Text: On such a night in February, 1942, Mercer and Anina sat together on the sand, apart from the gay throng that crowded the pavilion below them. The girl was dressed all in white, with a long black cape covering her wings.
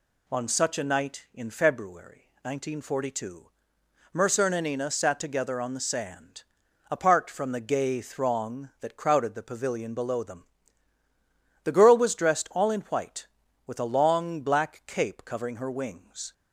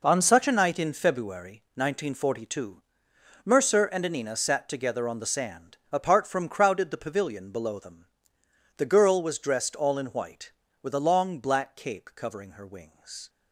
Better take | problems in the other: first | skips "the gay throng that"; at 6.4 s

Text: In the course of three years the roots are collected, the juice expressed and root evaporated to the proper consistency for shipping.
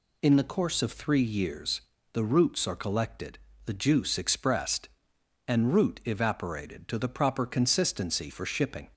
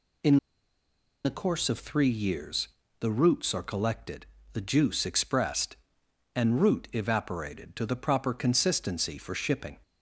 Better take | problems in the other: first | pauses between "In" and "the"; noticeable; at 0.3 s; 0.88 s long // pauses between "years" and "the"; slight; at 2.6 s; 0.32 s long; slight in the first

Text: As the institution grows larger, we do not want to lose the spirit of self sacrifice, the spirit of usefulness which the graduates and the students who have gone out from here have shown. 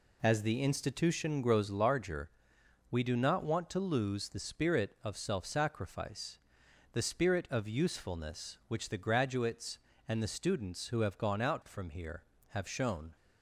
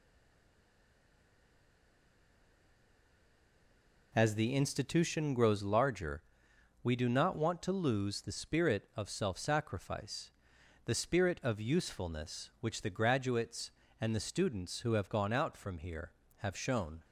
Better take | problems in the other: first | stays silent before the first word; strong; until 4.1 s; 4.1 s long

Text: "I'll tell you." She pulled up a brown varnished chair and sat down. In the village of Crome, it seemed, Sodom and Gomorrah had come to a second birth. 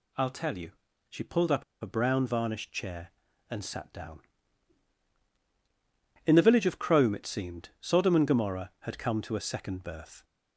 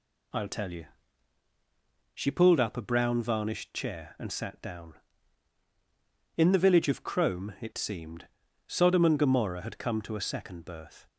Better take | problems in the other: second | pauses between "up" and "a"; slight; at 1.6 s; 0.18 s long

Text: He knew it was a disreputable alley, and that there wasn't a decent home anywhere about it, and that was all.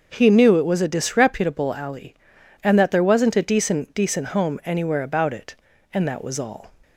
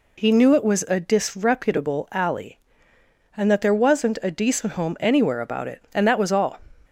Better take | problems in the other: second | starts louder than the rest; until 1.1 s; 6.5 dB // says "decent" twice; at 3.9 s

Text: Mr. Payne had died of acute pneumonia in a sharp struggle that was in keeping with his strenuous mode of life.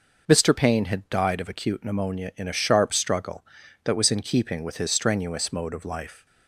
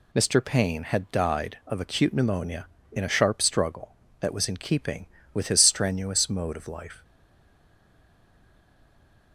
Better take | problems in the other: first | stays silent after the last word; from 7.0 s on; 2.3 s long

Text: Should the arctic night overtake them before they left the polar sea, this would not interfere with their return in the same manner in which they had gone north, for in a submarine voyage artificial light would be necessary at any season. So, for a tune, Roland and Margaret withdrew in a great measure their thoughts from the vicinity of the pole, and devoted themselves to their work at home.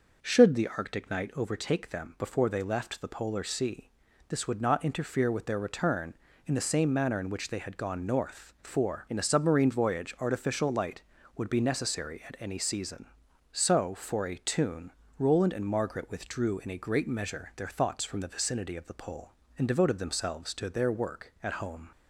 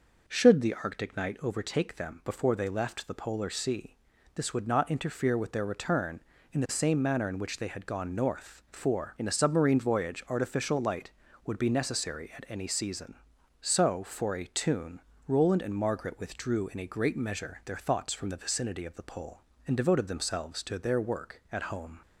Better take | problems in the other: neither | none

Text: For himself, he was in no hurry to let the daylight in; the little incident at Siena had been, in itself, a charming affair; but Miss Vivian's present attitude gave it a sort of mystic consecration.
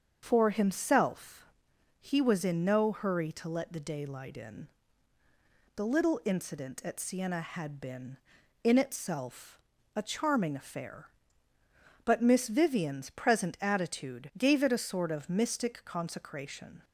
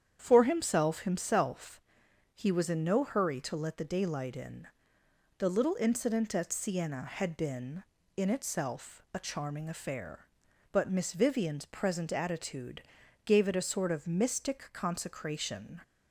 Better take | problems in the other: first | starts louder than the rest; strong; until 1.2 s; 9 dB; also in the first // says "himself" twice; at 1.0 s // pauses between "attitude" and "gave"; at 12.8 s; 0.42 s long

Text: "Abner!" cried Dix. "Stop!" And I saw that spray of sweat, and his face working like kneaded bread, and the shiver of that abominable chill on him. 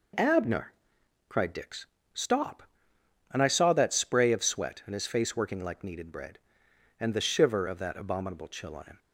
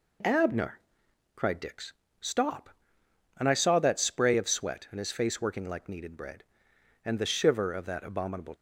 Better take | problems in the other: first | stops before "chill on him"; at 8.5 s

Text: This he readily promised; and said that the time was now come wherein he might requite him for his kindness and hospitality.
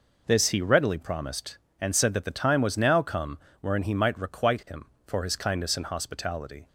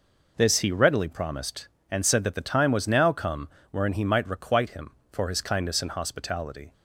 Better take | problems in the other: neither | pauses between "come" and "wherein"; slight; the same in both

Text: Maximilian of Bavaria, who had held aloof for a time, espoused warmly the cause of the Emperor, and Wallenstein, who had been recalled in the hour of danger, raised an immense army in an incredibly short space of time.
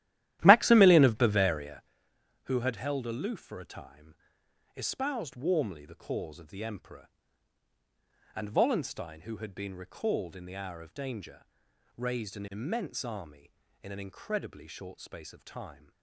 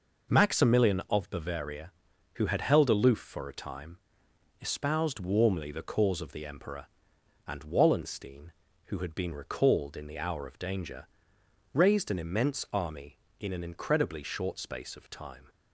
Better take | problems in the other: second | starts louder than the rest; strong; until 1.9 s; 13.5 dB

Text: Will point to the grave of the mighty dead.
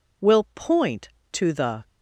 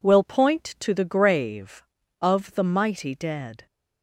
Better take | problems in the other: second | stops before "grave of the mighty dead"; at 1.8 s

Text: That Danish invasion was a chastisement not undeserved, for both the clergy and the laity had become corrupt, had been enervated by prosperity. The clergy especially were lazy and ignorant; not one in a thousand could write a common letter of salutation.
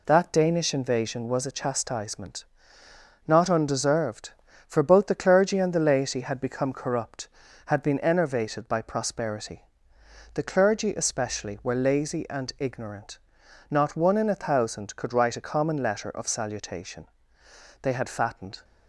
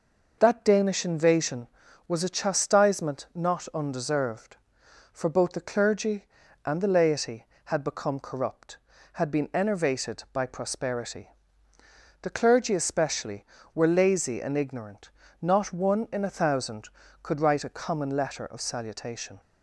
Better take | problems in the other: second | pauses between "chastisement" and "not"; noticeable; at 2.4 s; 0.84 s long // goes on to say "They had fattened"; noticeable; from 17.8 s on; 0.82 s long

